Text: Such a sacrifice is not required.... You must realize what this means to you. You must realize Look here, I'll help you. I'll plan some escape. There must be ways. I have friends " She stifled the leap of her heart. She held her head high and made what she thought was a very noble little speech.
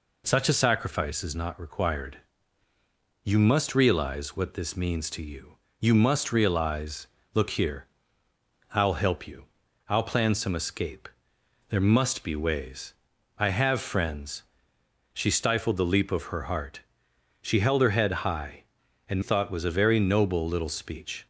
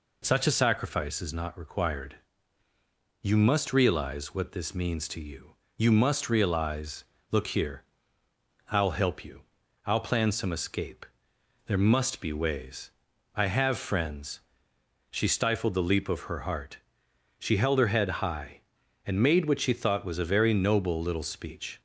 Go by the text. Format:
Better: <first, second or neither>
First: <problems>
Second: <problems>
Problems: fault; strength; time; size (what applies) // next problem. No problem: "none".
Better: second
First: pauses between "realize" and "Look"; slight; at 7.0 s; 0.30 s long // skips "made what she"; at 19.2 s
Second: pauses between "realize" and "Look"; slight; at 7.0 s; 0.30 s long